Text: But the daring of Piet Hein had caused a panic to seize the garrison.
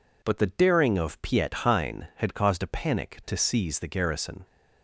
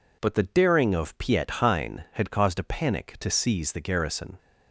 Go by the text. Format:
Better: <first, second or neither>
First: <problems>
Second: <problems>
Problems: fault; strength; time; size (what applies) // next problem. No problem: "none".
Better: neither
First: none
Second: none